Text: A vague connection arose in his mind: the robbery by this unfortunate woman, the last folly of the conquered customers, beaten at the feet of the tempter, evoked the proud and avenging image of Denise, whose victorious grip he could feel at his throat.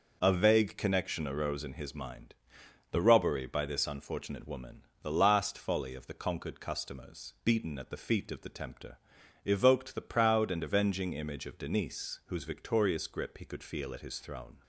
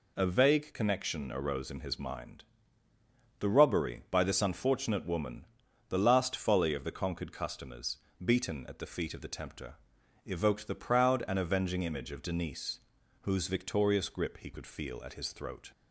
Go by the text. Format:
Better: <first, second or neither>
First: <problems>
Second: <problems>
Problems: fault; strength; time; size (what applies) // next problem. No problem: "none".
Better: second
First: says "throne" for "throat"; at 14.1 s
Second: none